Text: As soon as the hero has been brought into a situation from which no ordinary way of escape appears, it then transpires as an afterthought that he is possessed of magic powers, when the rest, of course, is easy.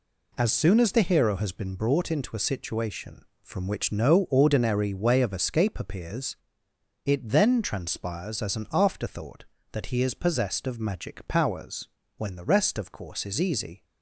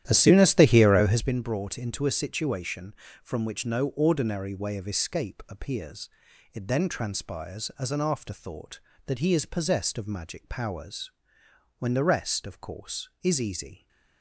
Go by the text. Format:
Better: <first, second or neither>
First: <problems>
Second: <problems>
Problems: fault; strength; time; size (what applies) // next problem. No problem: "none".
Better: first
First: none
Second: starts louder than the rest; strong; until 1.3 s; 11.5 dB